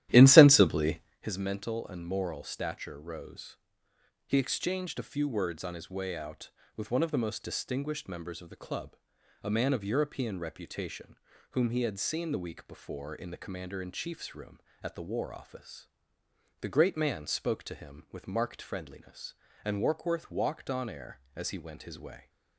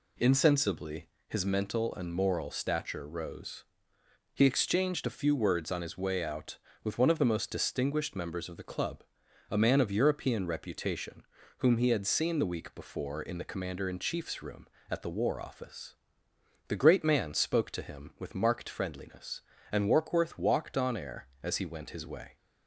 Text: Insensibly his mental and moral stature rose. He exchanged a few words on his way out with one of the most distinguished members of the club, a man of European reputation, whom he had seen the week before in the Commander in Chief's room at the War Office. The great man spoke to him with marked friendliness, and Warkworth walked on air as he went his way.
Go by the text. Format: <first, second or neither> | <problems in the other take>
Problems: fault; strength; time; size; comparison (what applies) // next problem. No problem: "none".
second | starts louder than the rest; strong; until 1.3 s; 13 dB // pauses between "Insensibly" and "his"; slight; at 1.0 s; 0.20 s long; slight in the second